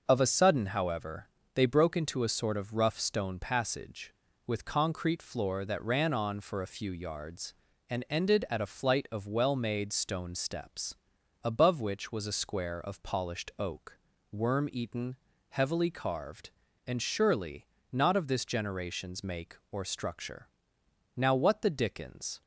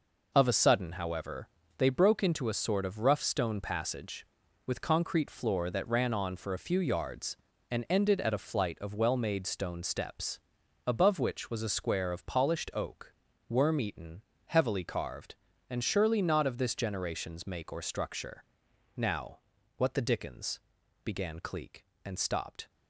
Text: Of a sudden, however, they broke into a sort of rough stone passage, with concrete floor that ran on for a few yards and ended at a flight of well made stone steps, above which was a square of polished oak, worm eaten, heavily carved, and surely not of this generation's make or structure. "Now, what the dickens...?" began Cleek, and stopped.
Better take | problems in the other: second | pauses between "surely" and "not"; slight; at 17.6 s; 0.26 s long // stops before "began Cleek and stopped"; at 22.4 s

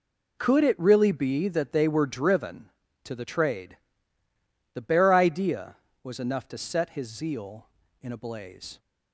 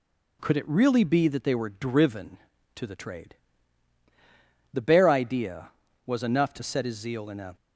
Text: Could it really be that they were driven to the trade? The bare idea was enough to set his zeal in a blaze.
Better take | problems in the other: first | stops before "blaze"; at 7.5 s

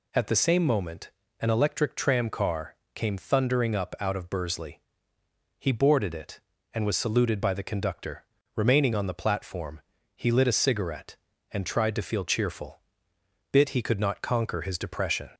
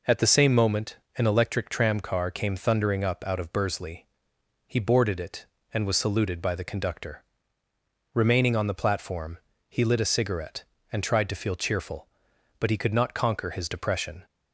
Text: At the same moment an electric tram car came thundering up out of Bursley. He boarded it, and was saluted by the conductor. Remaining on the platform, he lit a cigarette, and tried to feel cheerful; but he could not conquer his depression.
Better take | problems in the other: second | pauses between "moment" and "an"; slight; at 1.0 s; 0.28 s long; slight in the second // pauses between "car" and "came"; slight; at 2.7 s; 0.22 s long // says "bit" for "but"; at 13.5 s

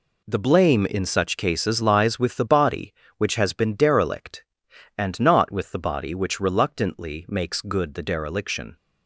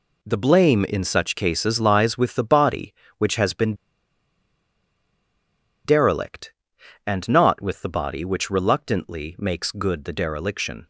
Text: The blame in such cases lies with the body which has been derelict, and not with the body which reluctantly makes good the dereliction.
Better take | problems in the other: first | pauses between "been" and "derelict"; strong; at 3.7 s; 2.1 s long

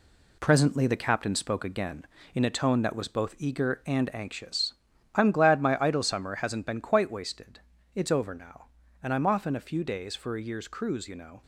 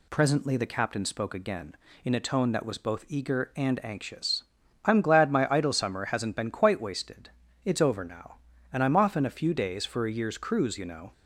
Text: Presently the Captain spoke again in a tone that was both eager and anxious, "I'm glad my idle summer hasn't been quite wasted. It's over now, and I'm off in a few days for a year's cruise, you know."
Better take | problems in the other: second | gets quieter; throughout; 7 dB

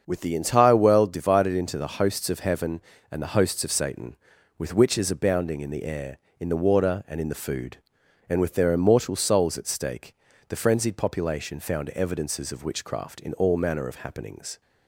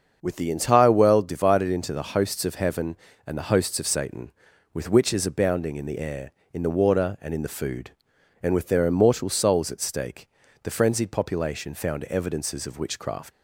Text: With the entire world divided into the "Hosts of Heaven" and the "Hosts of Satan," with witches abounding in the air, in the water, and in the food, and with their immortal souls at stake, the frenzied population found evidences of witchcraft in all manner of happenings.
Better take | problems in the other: first | starts louder than the rest; until 1.2 s; 6.5 dB; also in the first // stops before "in all manner of happenings"; at 13.3 s

